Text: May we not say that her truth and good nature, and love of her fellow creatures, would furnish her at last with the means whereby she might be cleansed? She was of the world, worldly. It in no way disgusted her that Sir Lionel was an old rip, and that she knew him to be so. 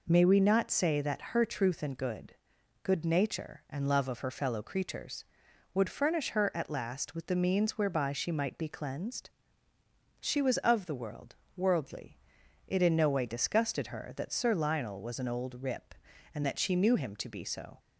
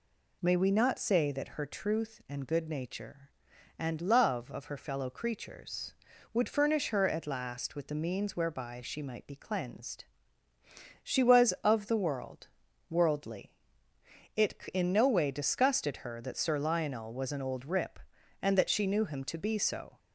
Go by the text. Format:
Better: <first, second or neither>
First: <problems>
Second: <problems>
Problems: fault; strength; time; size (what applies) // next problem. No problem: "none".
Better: second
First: says "good" twice; at 2.8 s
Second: none